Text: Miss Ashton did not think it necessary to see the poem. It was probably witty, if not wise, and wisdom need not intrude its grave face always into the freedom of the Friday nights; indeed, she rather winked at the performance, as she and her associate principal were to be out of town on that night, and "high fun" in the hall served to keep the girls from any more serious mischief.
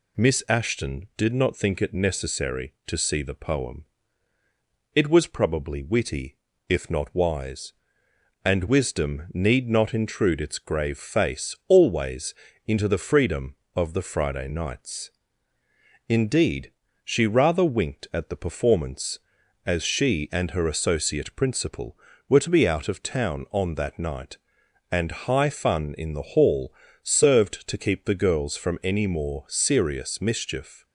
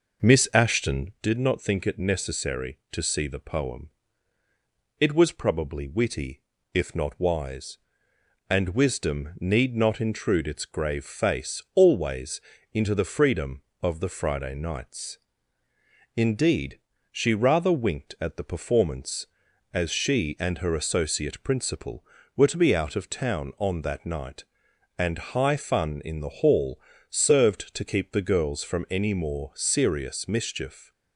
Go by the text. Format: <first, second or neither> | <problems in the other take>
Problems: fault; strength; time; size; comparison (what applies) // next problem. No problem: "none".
first | starts louder than the rest; noticeable; until 1.2 s; 5.5 dB // pauses between "always" and "into"; slight; at 12.4 s; 0.32 s long; slight in the first // pauses between "hall" and "served"; slight; at 26.7 s; 0.32 s long; slight in the first